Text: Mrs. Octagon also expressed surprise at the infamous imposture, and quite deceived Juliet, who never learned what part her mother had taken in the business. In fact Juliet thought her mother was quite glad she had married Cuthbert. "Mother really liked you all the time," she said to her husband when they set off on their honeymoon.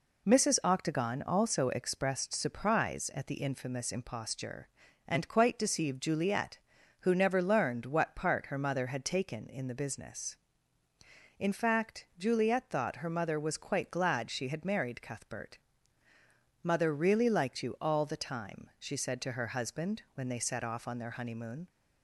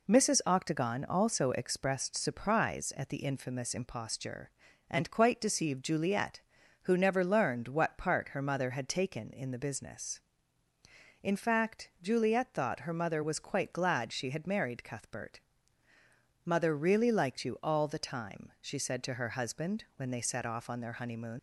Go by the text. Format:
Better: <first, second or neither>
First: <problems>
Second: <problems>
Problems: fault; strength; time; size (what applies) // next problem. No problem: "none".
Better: first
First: none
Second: leaves "honeymoon" unfinished; at 21.3 s; 110 ms